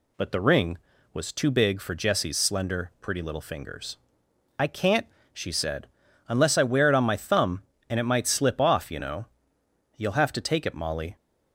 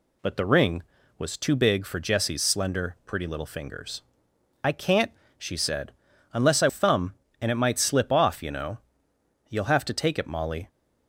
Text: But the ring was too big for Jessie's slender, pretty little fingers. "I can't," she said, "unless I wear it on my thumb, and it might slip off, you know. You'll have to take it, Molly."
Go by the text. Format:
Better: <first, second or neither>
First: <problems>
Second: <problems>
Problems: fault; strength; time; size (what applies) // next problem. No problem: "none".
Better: first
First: none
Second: skips "wear it on my"; at 6.6 s